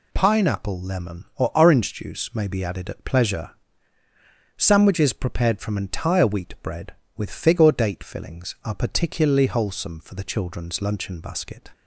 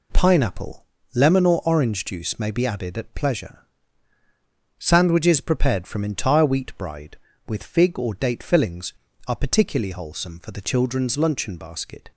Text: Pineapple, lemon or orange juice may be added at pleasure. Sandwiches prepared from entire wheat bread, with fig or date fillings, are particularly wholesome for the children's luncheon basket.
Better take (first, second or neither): first